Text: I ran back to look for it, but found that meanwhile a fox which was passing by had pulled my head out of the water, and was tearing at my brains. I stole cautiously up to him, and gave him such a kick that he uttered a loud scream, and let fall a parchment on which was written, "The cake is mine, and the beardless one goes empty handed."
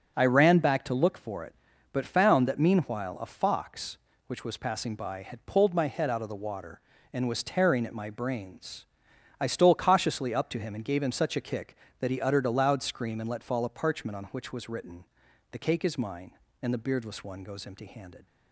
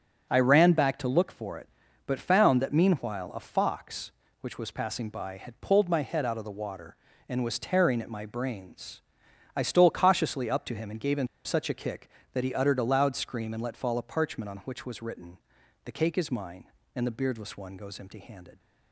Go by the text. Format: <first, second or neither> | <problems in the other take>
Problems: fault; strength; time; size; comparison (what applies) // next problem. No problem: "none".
first | starts louder than the rest; until 1.3 s; 6.5 dB; also in the first // pauses between "him" and "such"; slight; at 11.2 s; 0.18 s long